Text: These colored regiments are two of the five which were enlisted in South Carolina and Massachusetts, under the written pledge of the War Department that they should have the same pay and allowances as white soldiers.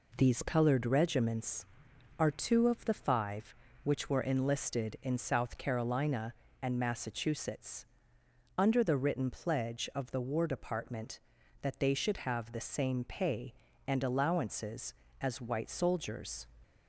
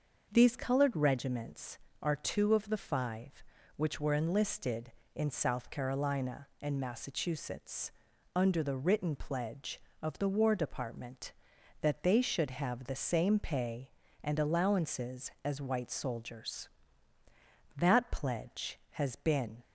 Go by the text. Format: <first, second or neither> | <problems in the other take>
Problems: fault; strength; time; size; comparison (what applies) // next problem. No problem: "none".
first | starts louder than the rest; until 1.3 s; 6.5 dB // goes on to say "That pledge has been"; strong; from 17.7 s on; 1.8 s long